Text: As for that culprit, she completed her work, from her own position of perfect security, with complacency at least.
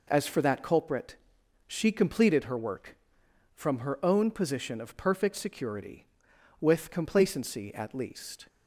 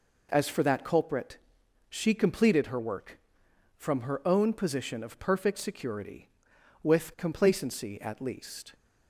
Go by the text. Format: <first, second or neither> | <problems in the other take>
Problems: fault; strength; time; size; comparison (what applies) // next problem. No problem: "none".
neither | none